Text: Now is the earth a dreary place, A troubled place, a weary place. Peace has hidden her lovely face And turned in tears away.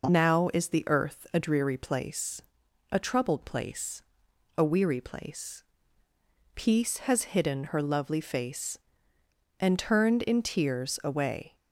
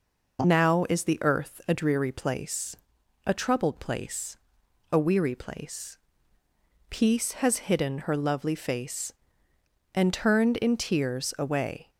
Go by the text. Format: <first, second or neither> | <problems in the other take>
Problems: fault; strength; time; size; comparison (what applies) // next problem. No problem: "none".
neither | none